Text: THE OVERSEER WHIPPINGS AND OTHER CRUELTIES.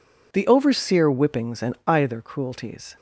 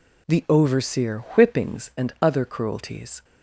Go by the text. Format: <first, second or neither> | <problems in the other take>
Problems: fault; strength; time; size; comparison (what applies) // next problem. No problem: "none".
second | says "Either" for "OTHER"; at 1.8 s